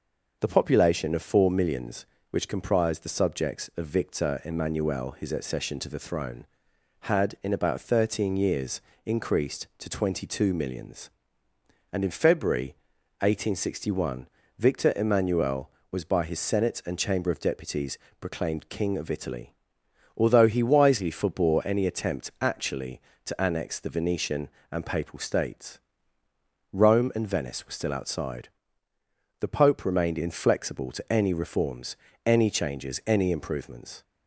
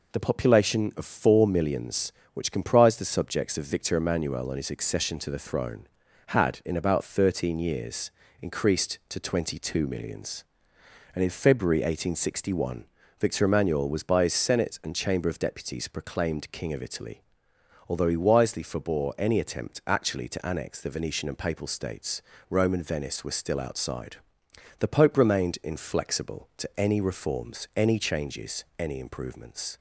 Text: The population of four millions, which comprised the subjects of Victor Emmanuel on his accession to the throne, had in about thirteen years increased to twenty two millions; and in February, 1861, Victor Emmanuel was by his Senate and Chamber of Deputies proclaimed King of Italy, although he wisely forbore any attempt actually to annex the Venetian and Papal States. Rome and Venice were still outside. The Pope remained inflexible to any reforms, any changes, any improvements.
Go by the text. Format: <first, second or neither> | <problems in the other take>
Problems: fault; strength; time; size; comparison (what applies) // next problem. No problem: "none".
second | skips "on"; at 5.1 s // pauses between "years" and "increased"; slight; at 8.8 s; 0.24 s long; slight in the second // pauses between "Deputies" and "proclaimed"; slight; at 17.9 s; 0.24 s long